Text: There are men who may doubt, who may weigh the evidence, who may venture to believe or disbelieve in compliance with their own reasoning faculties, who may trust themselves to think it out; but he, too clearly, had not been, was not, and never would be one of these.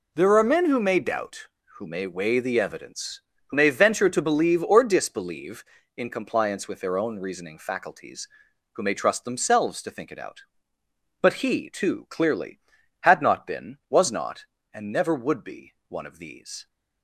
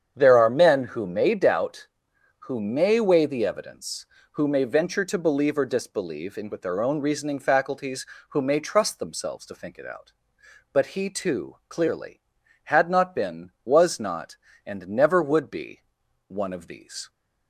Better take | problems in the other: first | starts louder than the rest; strong; until 1.1 s; 8 dB // skips "compliance"; at 6.5 s // pauses between "be" and "one"; noticeable; at 15.8 s; 0.46 s long

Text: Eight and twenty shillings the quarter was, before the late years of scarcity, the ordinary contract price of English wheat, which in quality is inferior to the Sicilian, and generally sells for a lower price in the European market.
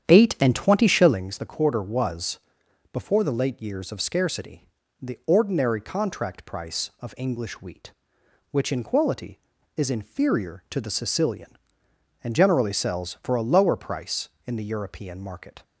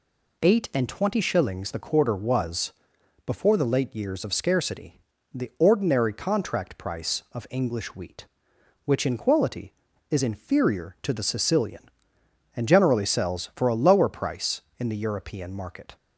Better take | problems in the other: second | starts louder than the rest; strong; until 1.3 s; 9 dB

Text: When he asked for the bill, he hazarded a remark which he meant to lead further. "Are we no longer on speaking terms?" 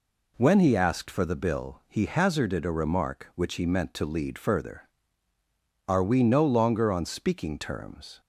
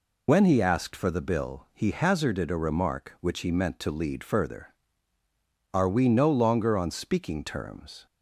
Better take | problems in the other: first | loses the start of "When"; at 0.2 s; 70 ms

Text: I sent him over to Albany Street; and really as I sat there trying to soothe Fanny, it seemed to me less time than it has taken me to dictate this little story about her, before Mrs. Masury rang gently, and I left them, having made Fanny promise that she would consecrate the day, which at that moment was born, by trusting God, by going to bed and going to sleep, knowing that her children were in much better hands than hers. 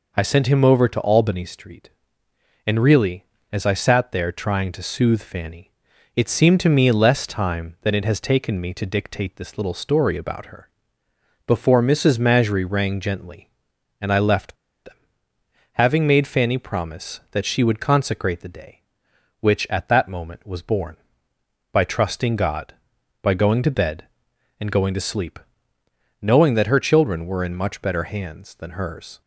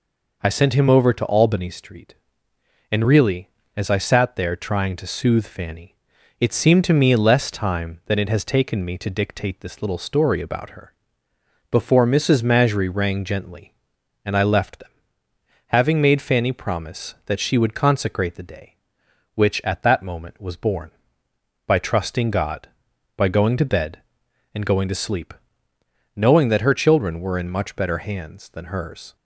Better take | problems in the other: second | pauses between "left" and "them"; slight; at 14.5 s; 0.32 s long

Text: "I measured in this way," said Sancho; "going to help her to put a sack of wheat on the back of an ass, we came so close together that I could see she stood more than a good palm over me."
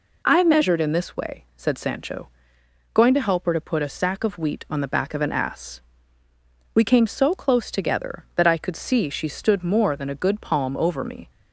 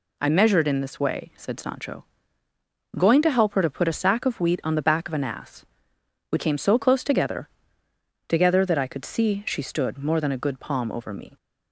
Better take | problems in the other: first | says "together" twice; at 8.2 s

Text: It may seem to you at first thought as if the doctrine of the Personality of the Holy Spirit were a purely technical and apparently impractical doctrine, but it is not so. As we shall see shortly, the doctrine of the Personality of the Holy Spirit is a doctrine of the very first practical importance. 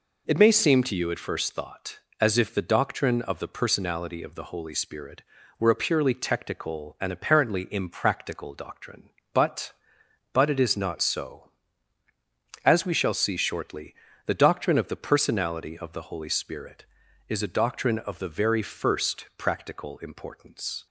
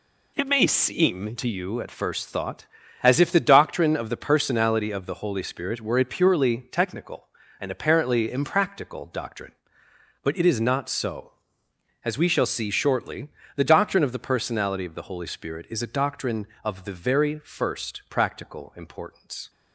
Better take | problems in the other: second | says "but" twice; at 10.3 s

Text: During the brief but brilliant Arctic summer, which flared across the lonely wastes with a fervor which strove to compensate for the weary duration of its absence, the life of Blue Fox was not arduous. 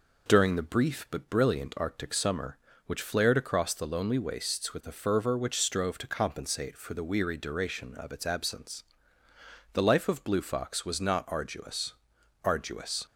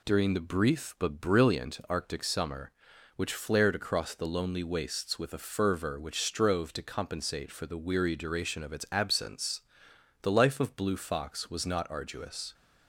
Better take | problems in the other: second | says "arduous" twice; at 12.4 s

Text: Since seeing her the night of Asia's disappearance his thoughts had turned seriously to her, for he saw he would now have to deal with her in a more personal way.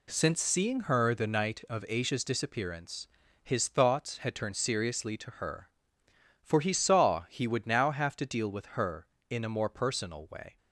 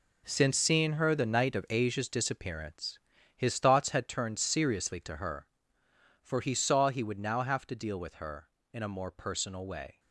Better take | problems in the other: first | gets quieter; strong; throughout; 10.5 dB // pauses between "disappearance" and "his"; at 2.9 s; 0.38 s long; slight in the first

